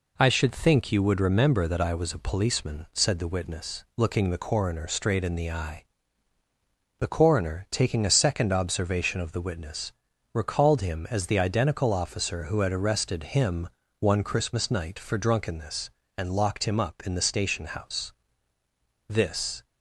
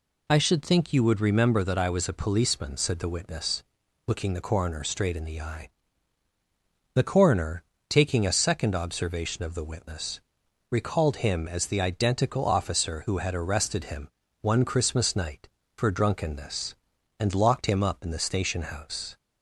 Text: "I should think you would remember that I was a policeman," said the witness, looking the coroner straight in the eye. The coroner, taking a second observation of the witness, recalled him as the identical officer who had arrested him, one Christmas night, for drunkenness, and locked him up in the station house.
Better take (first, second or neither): second